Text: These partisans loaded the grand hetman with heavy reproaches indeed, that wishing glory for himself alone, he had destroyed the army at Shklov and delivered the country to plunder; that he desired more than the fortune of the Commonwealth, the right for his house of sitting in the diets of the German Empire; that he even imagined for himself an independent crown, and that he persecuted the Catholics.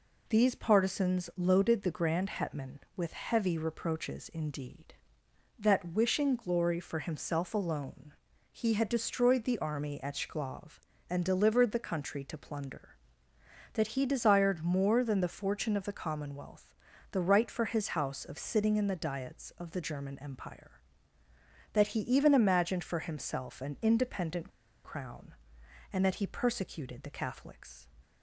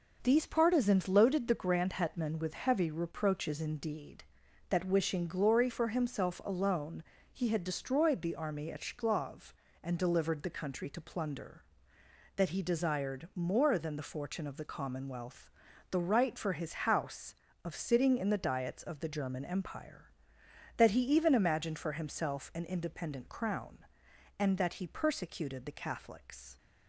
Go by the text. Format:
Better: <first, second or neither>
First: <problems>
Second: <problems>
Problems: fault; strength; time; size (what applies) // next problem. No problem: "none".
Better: second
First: pauses between "independent" and "crown"; slight; at 24.5 s; 0.34 s long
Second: none